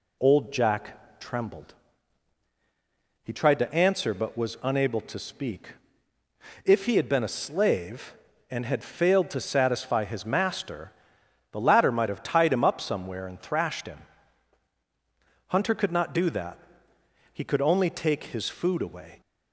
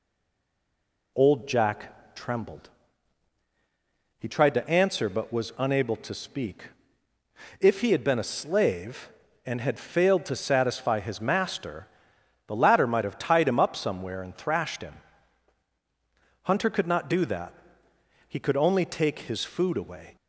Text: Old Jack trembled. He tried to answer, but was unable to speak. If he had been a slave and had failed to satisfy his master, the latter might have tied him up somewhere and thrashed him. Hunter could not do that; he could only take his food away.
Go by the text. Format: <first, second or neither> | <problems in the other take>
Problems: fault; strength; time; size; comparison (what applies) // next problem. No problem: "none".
first | stays silent before the first word; until 1.1 s; 1.1 s long